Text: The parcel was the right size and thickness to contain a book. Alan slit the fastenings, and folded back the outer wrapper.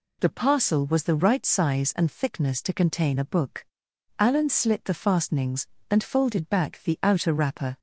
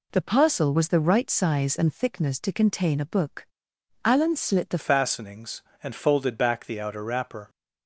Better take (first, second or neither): first